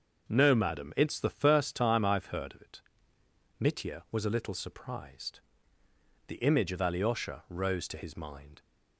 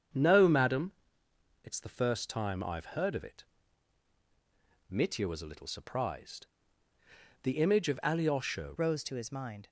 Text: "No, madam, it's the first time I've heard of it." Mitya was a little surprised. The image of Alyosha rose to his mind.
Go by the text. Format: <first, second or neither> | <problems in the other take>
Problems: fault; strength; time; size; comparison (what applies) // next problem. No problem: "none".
first | starts louder than the rest; strong; until 1.8 s; 7.5 dB; also in the first // changes voice at "rose"; from 8.7 s on; 0.9 s long